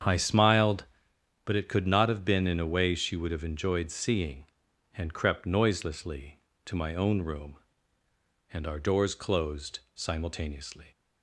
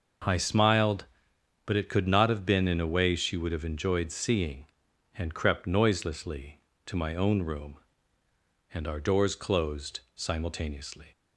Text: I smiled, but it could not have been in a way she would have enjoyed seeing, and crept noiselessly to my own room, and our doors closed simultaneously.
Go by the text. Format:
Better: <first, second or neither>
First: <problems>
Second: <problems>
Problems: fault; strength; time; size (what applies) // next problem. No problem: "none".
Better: second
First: starts louder than the rest; strong; until 1.1 s; 8 dB // pauses between "closed" and "simultaneously"; slight; at 9.7 s; 0.16 s long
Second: pauses between "closed" and "simultaneously"; slight; at 9.9 s; 0.16 s long